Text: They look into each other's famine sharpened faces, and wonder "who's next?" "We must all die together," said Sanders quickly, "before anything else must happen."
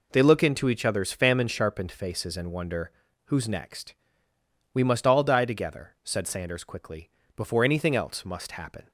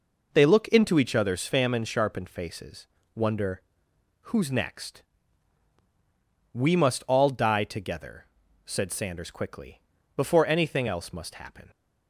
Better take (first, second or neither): first